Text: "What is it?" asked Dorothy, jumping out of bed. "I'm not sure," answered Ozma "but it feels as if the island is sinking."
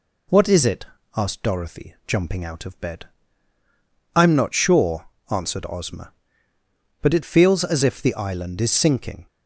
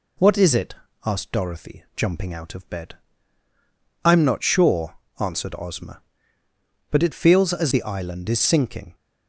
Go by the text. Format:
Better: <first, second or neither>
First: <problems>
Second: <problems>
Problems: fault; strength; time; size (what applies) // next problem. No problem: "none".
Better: first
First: none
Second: skips "if"; at 7.7 s